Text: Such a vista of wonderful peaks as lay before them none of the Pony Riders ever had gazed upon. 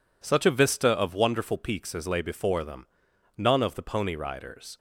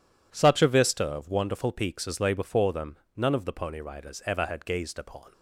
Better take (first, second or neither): second